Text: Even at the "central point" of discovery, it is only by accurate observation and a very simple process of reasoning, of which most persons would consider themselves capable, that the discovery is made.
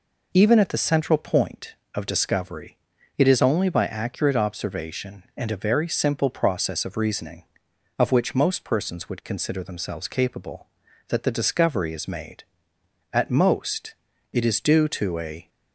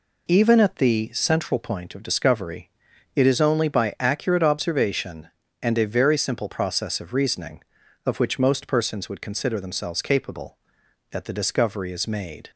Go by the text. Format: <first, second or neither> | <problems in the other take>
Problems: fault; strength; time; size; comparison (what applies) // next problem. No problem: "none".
second | goes on to say "At most it is due to a"; strong; from 13.1 s on; 2.3 s long